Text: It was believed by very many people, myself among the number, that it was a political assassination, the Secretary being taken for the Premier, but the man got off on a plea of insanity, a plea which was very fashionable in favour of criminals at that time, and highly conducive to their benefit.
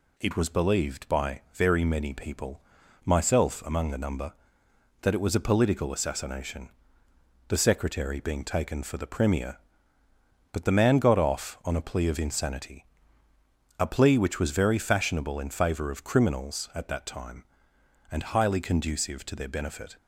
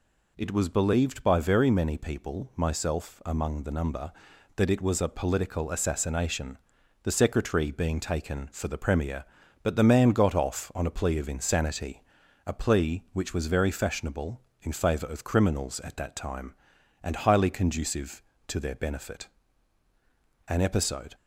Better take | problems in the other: first | goes on to say "An episode"; noticeable; from 20.4 s on; 0.66 s long

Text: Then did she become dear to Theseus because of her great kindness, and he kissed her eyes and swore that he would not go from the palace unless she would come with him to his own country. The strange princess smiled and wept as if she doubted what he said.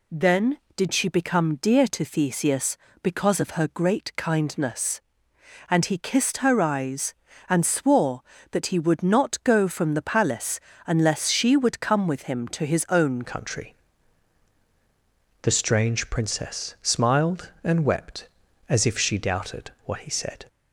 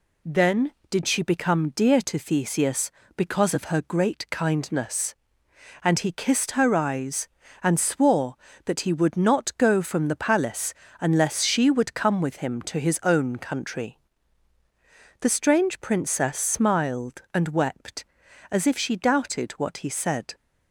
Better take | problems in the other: second | pauses between "palace" and "unless"; slight; at 10.5 s; 0.26 s long; slight in the second // changes voice at "country"; from 13.2 s on; 7.2 s long

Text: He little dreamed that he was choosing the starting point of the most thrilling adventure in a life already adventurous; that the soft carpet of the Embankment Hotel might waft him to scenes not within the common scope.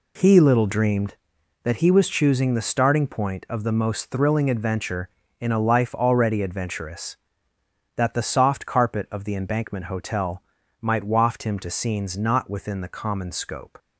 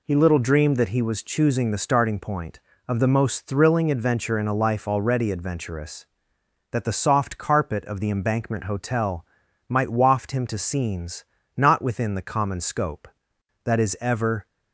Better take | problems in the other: first | pauses between "Hotel" and "might"; at 9.2 s; 0.44 s long; also in the first // pauses between "scenes" and "not"; slight; at 11.2 s; 0.32 s long // goes on to say "That is ever"; noticeable; from 13.6 s on; 0.82 s long

